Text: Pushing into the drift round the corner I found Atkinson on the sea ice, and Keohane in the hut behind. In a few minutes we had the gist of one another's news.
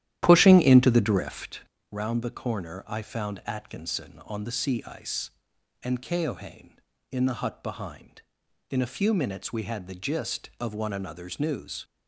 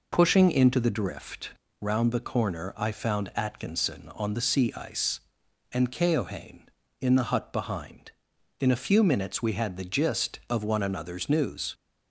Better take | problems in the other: second | starts louder than the rest; strong; until 1.6 s; 12 dB // pauses between "drift" and "round"; slight; at 1.5 s; 0.32 s long; slight in the second

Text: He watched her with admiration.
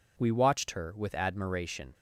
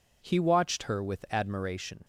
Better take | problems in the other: second | says "We" for "He"; at 0.1 s

